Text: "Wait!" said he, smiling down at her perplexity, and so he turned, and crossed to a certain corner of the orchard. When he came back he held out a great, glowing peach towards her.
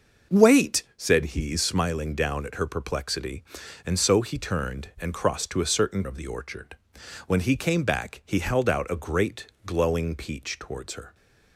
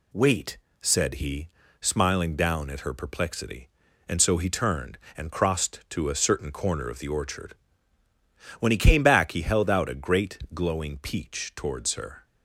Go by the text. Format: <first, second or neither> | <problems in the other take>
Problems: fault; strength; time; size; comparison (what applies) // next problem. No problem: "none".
second | starts louder than the rest; noticeable; until 1.4 s; 6 dB // skips "corner"; at 6.0 s